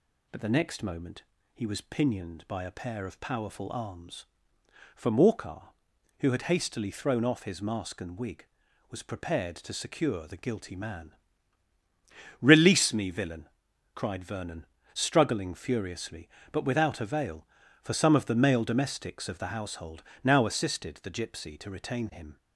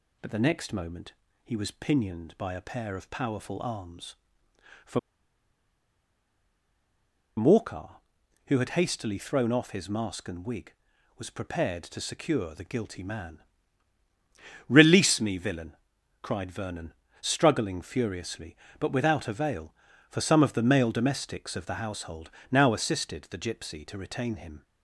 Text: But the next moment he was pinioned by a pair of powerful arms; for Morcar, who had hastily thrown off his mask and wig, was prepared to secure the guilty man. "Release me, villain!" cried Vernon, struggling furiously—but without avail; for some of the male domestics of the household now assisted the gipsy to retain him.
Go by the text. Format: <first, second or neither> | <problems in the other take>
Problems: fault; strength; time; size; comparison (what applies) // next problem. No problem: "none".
first | pauses between "moment" and "he"; slight; at 1.1 s; 0.32 s long; slight in the first // pauses between "for" and "Morcar"; strong; at 4.9 s; 2.3 s long // pauses between "household" and "now"; slight; at 22.2 s; 0.20 s long; slight in the first